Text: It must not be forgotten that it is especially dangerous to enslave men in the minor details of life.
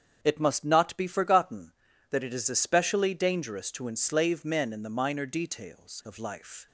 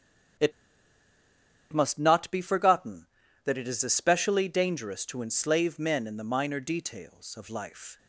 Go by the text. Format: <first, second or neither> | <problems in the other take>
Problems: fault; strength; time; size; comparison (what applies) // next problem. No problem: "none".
first | starts louder than the rest; strong; until 2.6 s; 7.5 dB; strong in the first // pauses between "It" and "must"; at 0.5 s; 1.2 s long